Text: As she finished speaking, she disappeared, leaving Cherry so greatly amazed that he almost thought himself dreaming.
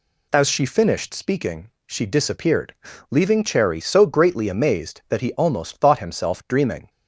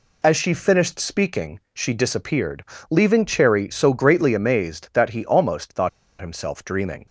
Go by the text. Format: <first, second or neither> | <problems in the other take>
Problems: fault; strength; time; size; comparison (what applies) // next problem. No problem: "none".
first | pauses between "thought" and "himself"; slight; at 5.8 s; 0.30 s long